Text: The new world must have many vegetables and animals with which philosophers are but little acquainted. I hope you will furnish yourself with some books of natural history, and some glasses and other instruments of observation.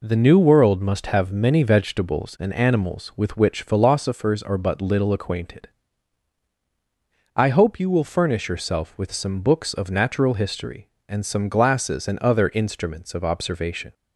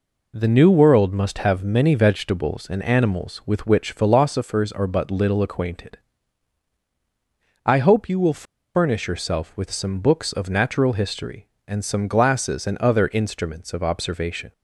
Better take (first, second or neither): first